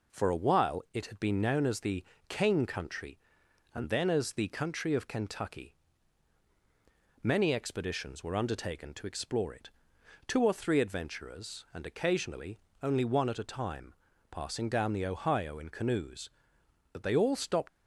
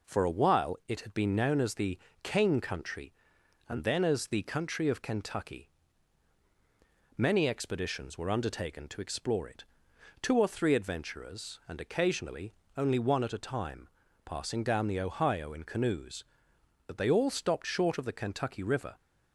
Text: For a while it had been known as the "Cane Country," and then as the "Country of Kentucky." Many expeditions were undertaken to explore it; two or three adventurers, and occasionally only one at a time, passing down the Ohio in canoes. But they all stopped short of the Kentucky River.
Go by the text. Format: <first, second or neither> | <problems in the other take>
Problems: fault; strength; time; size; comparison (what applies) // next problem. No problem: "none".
second | pauses between "the" and "Cane"; slight; at 2.0 s; 0.26 s long; slight in the second // pauses between "occasionally" and "only"; slight; at 12.5 s; 0.24 s long; slight in the second // stops before "short of the Kentucky River"; at 17.6 s